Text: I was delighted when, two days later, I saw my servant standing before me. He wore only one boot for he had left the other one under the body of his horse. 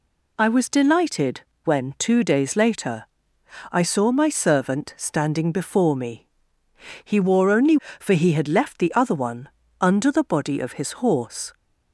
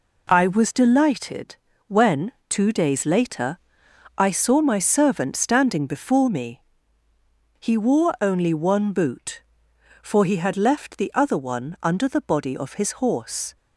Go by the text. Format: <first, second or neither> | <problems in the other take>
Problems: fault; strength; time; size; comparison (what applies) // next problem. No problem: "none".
second | pauses between "delighted" and "when"; slight; at 1.4 s; 0.24 s long; slight in the second // skips "one boot"; at 7.8 s // pauses between "one" and "under"; slight; at 9.4 s; 0.30 s long